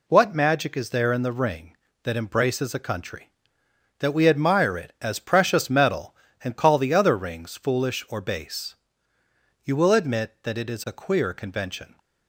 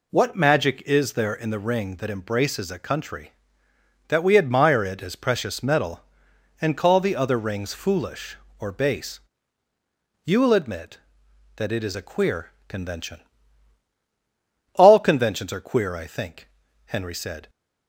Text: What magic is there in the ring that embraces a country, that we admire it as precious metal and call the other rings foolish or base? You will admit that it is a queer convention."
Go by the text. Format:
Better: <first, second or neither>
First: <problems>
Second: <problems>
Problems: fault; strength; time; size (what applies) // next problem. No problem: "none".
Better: first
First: none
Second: pauses between "queer" and "convention"; slight; at 12.5 s; 0.16 s long // goes on to say "All conventions are queer I think Henry said"; strong; from 14.7 s on; 2.7 s long